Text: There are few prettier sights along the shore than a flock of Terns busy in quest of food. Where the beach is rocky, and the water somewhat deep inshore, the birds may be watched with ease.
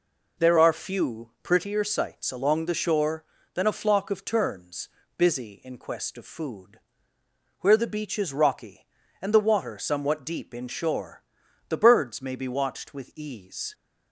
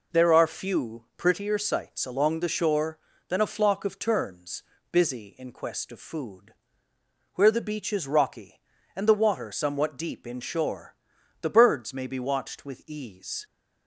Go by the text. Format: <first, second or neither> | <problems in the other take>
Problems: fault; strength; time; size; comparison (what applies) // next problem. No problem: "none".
neither | pauses between "Terns" and "busy"; slight; the same in both